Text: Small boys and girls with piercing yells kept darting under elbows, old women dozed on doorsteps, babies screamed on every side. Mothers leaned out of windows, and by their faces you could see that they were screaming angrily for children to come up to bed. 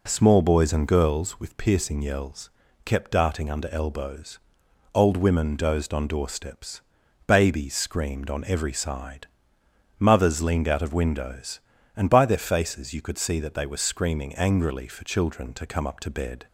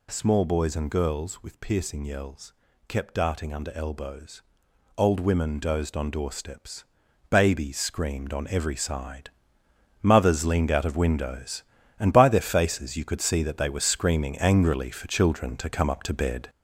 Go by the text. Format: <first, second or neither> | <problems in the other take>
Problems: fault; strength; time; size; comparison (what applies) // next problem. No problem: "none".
first | gets louder; noticeable; throughout; 6 dB // pauses between "yells" and "kept"; slight; at 2.5 s; 0.36 s long; slight in the first